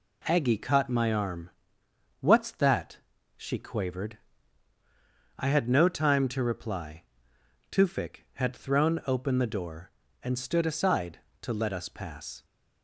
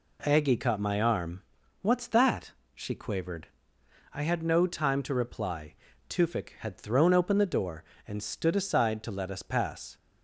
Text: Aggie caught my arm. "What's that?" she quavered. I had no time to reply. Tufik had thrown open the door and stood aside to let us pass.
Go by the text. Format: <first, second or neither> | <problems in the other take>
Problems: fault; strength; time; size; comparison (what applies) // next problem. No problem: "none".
neither | none